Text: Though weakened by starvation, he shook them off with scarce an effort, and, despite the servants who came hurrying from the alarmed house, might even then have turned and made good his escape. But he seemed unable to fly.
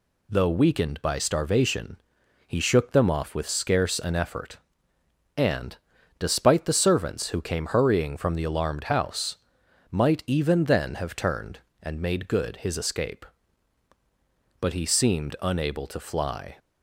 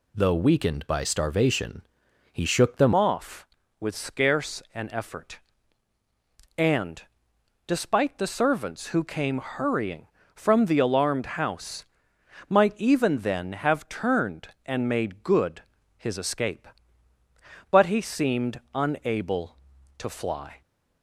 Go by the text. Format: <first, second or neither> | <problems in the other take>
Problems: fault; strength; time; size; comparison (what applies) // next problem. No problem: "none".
first | changes voice at "off"; from 2.9 s on; 17.7 s long // pauses between "good" and "his"; slight; at 15.6 s; 0.34 s long